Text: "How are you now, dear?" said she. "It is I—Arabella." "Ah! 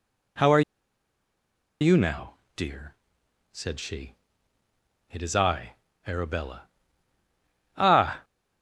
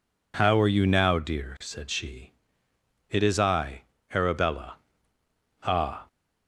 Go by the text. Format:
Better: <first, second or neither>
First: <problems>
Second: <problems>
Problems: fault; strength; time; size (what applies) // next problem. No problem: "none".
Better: second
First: pauses between "are" and "you"; at 0.6 s; 1.2 s long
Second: none